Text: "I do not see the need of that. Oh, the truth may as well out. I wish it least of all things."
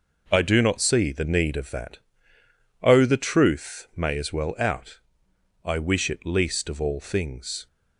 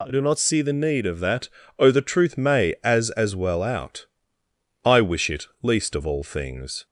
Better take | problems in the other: first | says "as" twice; at 3.1 s // pauses between "it" and "least"; slight; at 5.4 s; 0.16 s long

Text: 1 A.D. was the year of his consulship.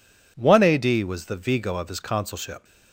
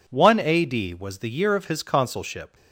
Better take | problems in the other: second | says "vigo" for "year"; at 1.3 s

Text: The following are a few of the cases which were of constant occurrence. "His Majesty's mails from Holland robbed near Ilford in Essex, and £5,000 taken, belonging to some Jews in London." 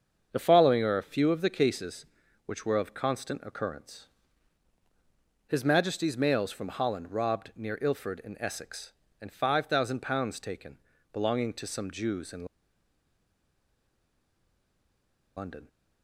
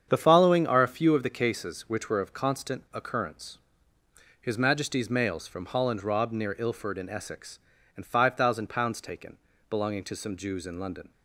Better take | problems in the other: second | starts louder than the rest; until 1.3 s; 7 dB; strong in the second // pauses between "in" and "London"; strong; at 12.4 s; 2.9 s long

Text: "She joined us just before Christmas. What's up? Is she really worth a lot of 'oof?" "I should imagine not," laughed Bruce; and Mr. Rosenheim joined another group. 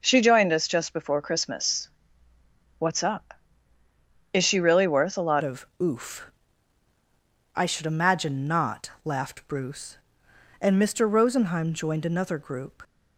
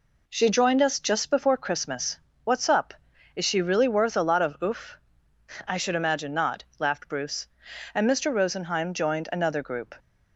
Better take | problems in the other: second | changes voice at "of"; from 5.4 s on; 7.4 s long // pauses between "of" and "oof"; slight; at 5.6 s; 0.16 s long

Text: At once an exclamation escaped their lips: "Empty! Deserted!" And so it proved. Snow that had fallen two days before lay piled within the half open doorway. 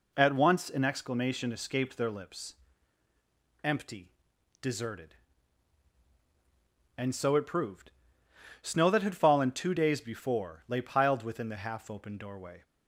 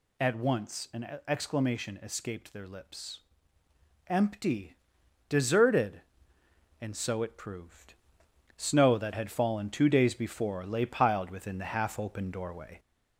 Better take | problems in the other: first | gets louder; slight; throughout; 2.5 dB

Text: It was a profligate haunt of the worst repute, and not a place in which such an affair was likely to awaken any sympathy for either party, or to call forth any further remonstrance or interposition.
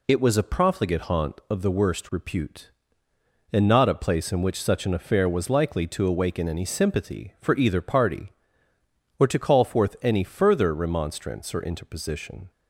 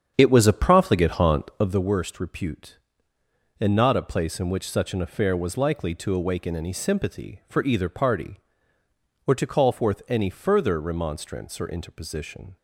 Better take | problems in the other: first | starts louder than the rest; strong; until 1.9 s; 8 dB

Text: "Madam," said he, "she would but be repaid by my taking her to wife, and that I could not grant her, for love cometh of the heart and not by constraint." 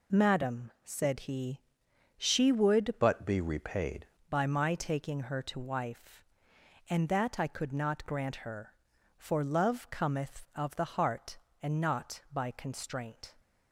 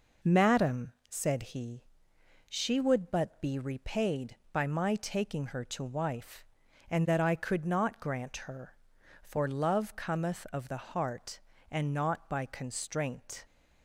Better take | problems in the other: second | changes voice from "but" to "repaid"; from 3.0 to 4.0 s; 1.0 s long

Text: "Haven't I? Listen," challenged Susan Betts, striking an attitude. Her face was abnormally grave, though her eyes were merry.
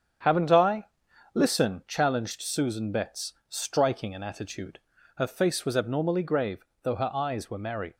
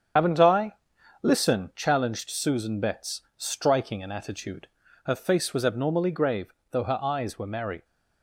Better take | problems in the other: first | loses the start of "Haven't"; at 0.1 s; 65 ms // starts louder than the rest; strong; until 1.6 s; 8 dB; strong in the first

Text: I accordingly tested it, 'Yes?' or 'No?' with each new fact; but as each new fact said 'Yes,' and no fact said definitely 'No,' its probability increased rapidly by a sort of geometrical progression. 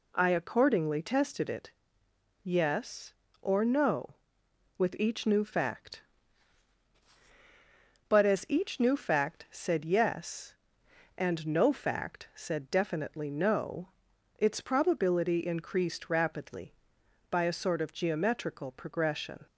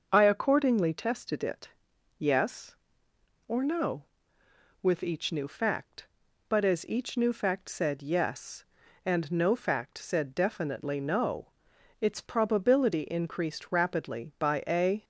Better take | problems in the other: first | starts louder than the rest; until 1.1 s; 6.5 dB // stops before "sort of geometrical progression"; at 15.0 s

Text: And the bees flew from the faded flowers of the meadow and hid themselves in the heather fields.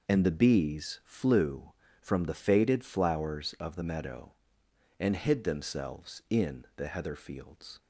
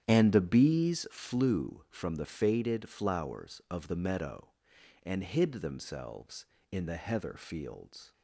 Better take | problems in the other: first | starts louder than the rest; strong; until 1.1 s; 10 dB

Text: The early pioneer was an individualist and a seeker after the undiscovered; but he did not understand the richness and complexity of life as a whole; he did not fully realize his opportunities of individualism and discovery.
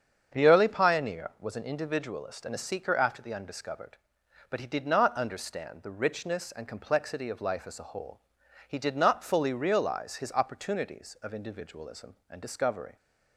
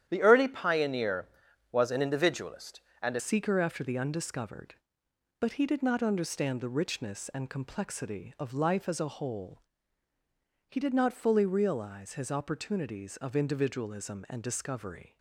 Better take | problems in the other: first | starts louder than the rest; strong; until 1.0 s; 10.5 dB; strong in the first // changes voice at "seeker"; from 3.1 s on; 12.0 s long

